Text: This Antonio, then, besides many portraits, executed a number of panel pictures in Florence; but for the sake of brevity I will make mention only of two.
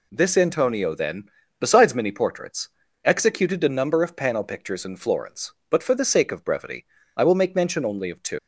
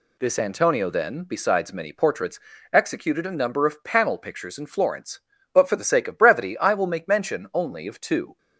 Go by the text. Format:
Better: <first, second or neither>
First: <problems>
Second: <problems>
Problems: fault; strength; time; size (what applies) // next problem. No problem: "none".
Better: second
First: pauses between "brevity" and "I"; slight; at 6.8 s; 0.28 s long // leaves "two" unfinished; at 8.3 s; 105 ms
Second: none